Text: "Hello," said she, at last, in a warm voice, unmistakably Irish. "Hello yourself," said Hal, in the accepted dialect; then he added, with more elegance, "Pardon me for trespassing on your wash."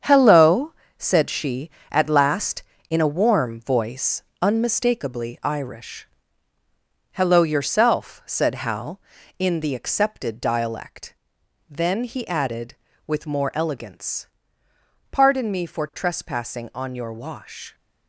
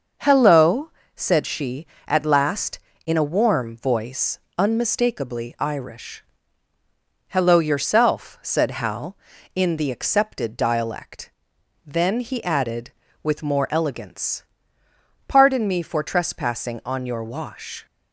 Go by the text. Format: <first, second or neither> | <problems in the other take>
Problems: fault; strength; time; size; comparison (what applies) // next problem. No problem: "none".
second | gets quieter; strong; throughout; 8 dB // starts louder than the rest; strong; until 1.2 s; 8 dB; also in the second